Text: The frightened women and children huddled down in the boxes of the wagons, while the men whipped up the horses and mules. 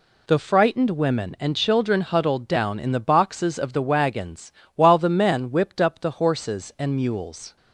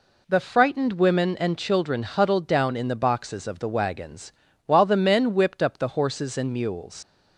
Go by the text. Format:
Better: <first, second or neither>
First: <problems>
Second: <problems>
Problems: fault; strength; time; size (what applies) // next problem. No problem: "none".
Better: first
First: none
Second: leaves "mules" unfinished; at 7.0 s; 95 ms